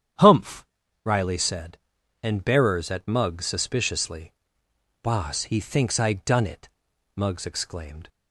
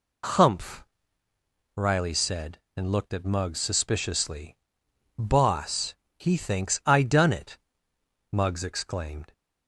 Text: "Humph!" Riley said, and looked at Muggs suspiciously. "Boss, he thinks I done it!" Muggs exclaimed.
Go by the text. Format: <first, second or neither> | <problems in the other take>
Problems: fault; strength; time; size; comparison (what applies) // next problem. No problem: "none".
second | starts louder than the rest; strong; until 1.5 s; 9 dB // says "bearers" for "looked"; at 2.4 s